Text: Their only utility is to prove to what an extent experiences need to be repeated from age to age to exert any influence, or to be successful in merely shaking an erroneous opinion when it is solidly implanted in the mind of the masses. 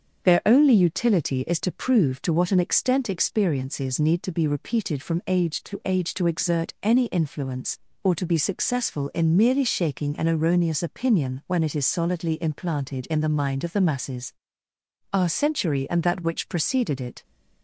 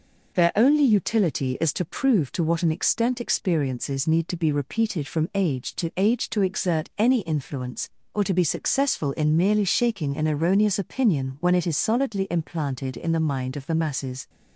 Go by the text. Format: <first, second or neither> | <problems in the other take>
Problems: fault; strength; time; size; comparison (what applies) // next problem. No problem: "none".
second | starts louder than the rest; until 1.2 s; 7 dB // goes on to say "Our century and that which preceded it"; strong; from 15.1 s on; 2.1 s long